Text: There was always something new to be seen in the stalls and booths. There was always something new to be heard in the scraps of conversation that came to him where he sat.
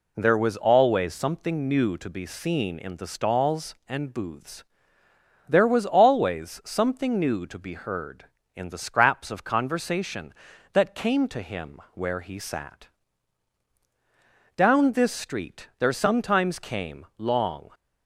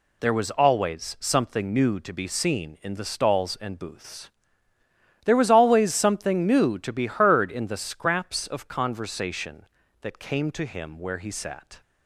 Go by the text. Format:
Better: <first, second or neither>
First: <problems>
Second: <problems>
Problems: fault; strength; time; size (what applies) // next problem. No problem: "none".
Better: second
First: goes on to say "Down this street there sometimes came long"; strong; from 14.5 s on; 3.1 s long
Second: none